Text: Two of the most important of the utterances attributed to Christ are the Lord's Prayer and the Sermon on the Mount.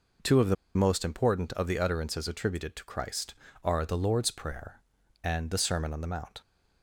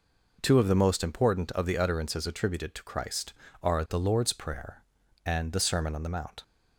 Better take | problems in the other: second | pauses between "the" and "most"; slight; at 0.5 s; 0.21 s long

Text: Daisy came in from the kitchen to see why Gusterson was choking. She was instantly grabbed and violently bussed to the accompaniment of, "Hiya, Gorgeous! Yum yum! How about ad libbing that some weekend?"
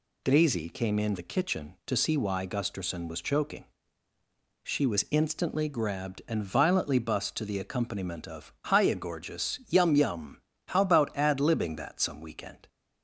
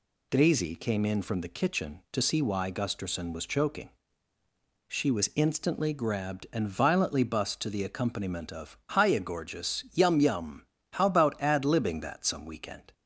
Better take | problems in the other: second | skips "from"; at 1.1 s

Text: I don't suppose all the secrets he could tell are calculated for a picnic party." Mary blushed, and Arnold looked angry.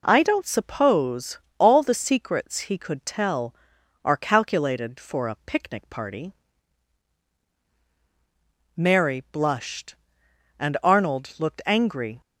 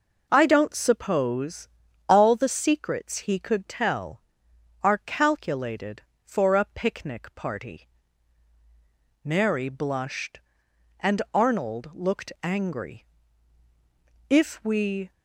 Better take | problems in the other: first | pauses between "suppose" and "all"; at 1.6 s; 0.38 s long; slight in the first // goes on to say "If we"; noticeable; from 14.2 s on; 0.84 s long

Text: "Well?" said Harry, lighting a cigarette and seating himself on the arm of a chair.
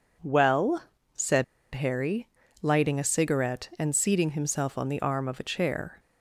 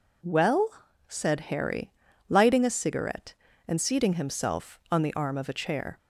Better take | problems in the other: second | pauses between "said" and "Harry"; slight; at 1.4 s; 0.30 s long

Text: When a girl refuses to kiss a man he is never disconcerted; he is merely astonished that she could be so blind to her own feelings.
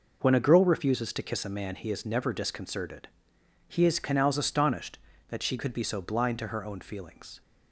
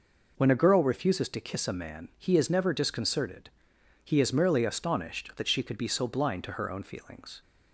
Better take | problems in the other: second | says "canals" for "merely"; at 3.9 s

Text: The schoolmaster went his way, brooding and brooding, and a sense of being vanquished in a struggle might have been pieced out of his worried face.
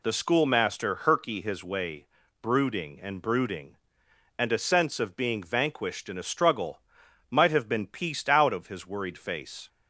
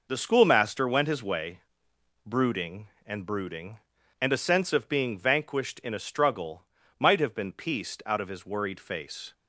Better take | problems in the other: second | says "herky" for "went"; at 0.9 s // pauses between "struggle" and "might"; noticeable; at 6.8 s; 0.50 s long; slight in the second

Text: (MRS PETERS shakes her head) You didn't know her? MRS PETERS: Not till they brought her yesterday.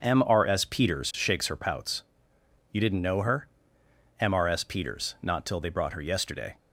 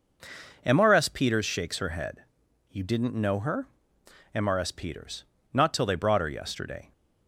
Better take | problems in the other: second | says "pouts" for "head"; at 1.5 s

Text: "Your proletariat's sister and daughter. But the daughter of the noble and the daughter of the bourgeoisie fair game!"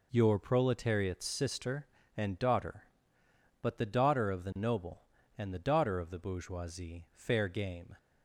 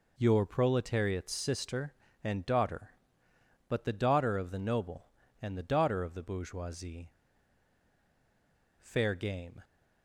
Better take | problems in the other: first | pauses between "bourgeoisie" and "fair"; strong; at 7.1 s; 1.7 s long

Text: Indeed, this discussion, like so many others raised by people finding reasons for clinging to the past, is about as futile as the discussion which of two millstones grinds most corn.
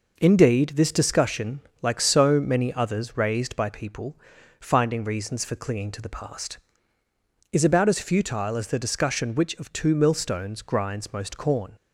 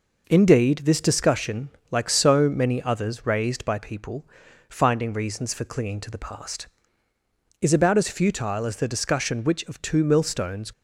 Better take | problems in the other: first | pauses between "people" and "finding"; at 4.2 s; 0.44 s long; also in the first // stops before "grinds most corn"; at 10.7 s

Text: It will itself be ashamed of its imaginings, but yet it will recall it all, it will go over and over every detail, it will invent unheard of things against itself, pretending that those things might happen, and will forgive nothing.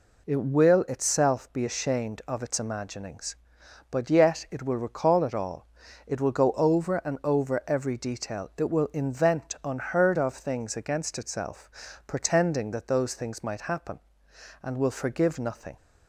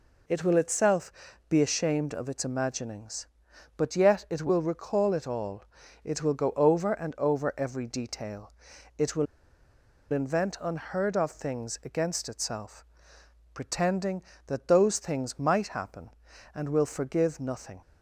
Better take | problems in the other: first | pauses between "itself" and "be"; at 1.1 s; 0.38 s long // pauses between "will" and "invent"; noticeable; at 9.2 s; 0.87 s long

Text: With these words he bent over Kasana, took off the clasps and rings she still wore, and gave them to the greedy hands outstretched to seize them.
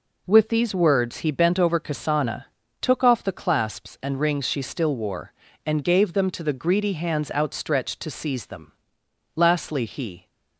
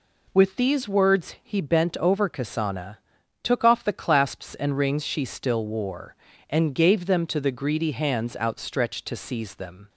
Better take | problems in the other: second | goes on to say "Lastly he"; noticeable; from 9.3 s on; 0.90 s long

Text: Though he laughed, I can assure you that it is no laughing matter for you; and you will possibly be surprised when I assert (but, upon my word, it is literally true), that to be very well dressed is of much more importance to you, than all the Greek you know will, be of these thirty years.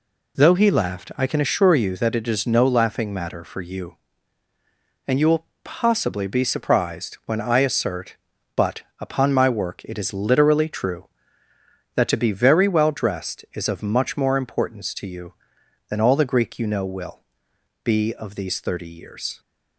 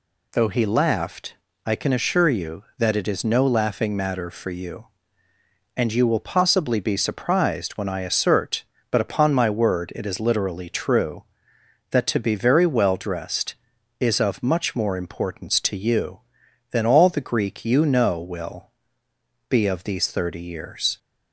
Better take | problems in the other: second | pauses between "will" and "possibly"; slight; at 5.4 s; 0.18 s long // says "work" for "word"; at 9.4 s

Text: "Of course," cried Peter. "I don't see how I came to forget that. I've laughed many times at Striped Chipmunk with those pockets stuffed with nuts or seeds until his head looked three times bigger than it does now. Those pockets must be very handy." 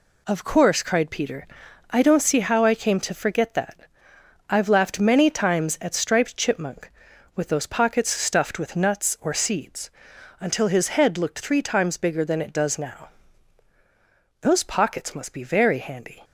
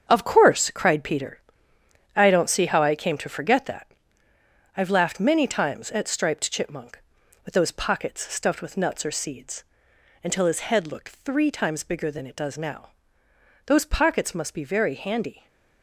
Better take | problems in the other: first | gets quieter; strong; throughout; 10 dB // pauses between "seeds" and "until"; noticeable; at 9.6 s; 0.60 s long; noticeable in the first // stays silent after the last word; slight; from 15.3 s on; 0.5 s long

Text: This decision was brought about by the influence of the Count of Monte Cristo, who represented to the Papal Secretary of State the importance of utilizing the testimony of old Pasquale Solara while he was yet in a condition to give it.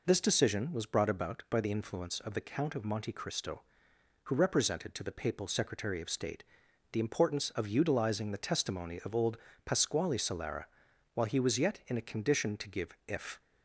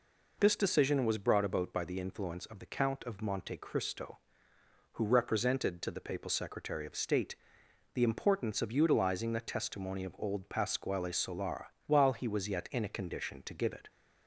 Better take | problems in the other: second | pauses between "State" and "the"; noticeable; at 6.4 s; 0.48 s long; noticeable in the second // pauses between "old" and "Pasquale"; slight; at 9.3 s; 0.28 s long // pauses between "Solara" and "while"; noticeable; at 10.6 s; 0.48 s long; slight in the second // says "if" for "it"; at 13.0 s

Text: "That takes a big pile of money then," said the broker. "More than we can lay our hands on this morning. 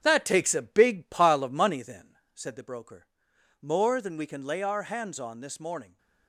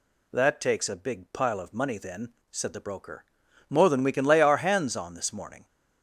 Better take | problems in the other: second | gets quieter; noticeable; throughout; 5 dB

